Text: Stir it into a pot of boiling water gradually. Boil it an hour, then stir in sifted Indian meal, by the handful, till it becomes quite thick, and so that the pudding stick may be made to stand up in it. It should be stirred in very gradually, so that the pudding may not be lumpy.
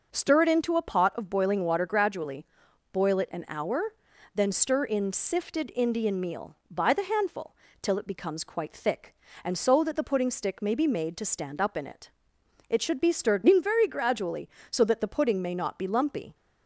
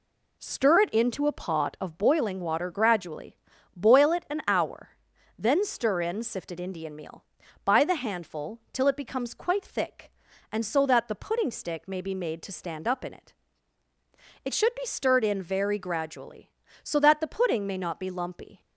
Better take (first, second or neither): neither